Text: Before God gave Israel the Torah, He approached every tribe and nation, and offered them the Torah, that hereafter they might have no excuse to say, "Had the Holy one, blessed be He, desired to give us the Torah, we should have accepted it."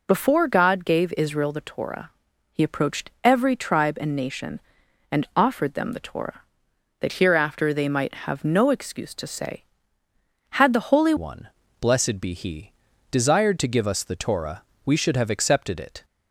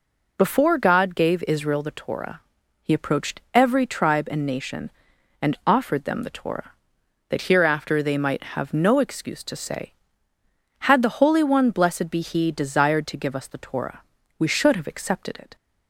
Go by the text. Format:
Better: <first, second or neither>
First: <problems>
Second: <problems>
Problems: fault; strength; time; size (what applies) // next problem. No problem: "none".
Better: second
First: changes voice at "one"; from 11.1 s on; 4.9 s long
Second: none